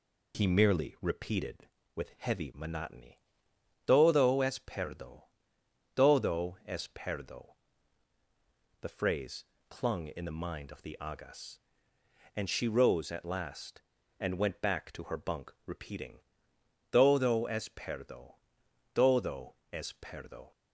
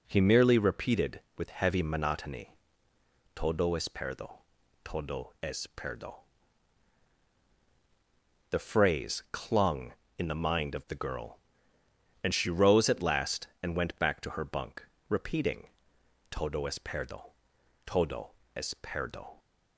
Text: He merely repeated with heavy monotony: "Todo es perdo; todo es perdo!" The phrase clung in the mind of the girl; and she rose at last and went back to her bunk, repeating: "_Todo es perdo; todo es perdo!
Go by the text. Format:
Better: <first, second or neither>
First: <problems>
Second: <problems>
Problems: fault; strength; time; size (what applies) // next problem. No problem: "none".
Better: second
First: pauses between "phrase" and "clung"; slight; at 9.4 s; 0.24 s long // says "agas" for "girl"; at 11.0 s // pauses between "todo" and "es"; slight; at 19.5 s; 0.18 s long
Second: pauses between "todo" and "es"; slight; at 18.3 s; 0.24 s long